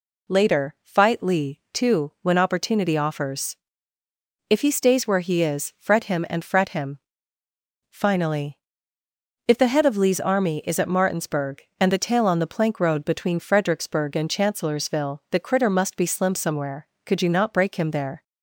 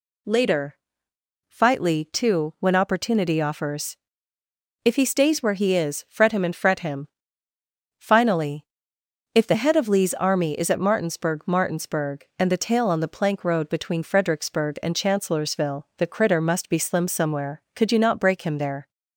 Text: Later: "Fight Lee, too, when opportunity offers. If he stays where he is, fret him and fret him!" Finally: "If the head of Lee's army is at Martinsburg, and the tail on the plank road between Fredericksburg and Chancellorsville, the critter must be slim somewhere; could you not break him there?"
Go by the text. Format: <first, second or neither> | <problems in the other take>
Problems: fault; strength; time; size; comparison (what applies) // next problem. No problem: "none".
first | says "Martinsburg" twice; at 11.4 s